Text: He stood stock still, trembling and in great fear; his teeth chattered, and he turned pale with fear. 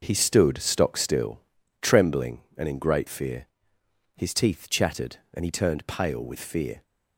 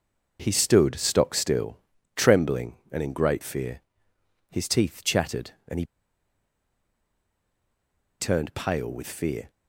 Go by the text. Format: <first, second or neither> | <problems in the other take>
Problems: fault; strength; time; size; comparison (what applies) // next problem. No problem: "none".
first | pauses between "he" and "turned"; strong; at 5.8 s; 2.3 s long